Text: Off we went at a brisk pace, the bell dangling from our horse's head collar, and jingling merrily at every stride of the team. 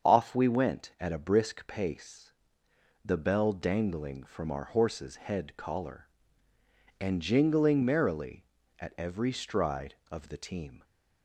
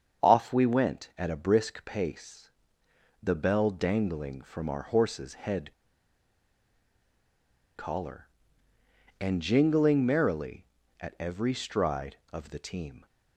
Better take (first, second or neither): first